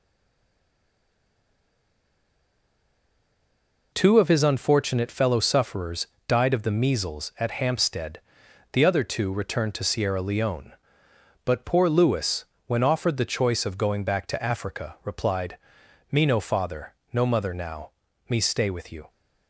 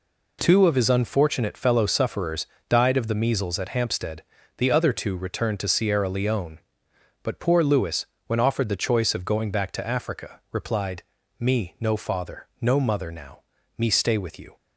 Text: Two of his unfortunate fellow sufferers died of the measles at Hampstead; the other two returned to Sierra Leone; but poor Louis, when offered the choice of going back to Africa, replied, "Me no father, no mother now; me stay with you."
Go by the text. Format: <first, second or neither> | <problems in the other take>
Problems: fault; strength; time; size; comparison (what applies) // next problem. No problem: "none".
second | stays silent before the first word; strong; until 3.9 s; 3.9 s long // pauses between "sufferers" and "died"; slight; at 6.0 s; 0.20 s long; slight in the second